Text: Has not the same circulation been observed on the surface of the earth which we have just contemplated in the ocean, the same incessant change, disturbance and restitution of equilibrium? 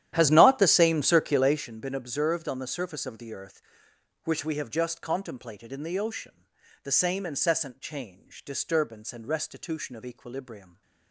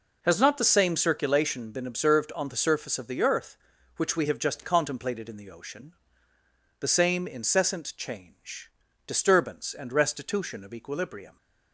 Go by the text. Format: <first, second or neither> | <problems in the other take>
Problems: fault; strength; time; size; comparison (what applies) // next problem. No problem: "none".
second | starts louder than the rest; strong; until 1.7 s; 11.5 dB